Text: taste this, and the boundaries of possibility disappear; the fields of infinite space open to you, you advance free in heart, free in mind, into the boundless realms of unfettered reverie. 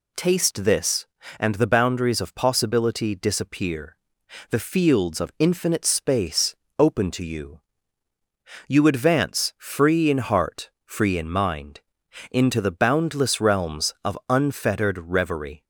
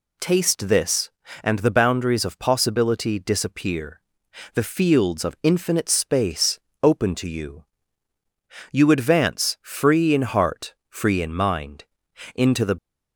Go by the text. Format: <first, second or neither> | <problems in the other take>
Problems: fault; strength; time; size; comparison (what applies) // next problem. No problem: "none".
first | pauses between "space" and "open"; slight; at 6.5 s; 0.22 s long; slight in the first // stops before "boundless realms of unfettered reverie"; at 12.7 s